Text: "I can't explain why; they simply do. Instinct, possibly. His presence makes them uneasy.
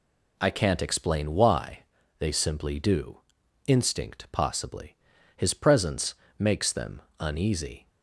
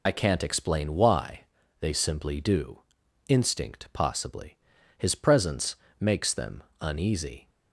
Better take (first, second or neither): first